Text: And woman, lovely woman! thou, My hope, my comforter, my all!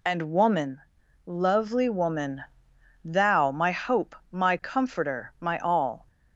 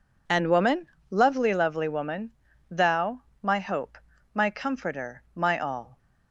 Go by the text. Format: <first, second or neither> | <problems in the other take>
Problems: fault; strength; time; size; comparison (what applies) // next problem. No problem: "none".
first | says "lovely" twice; at 1.5 s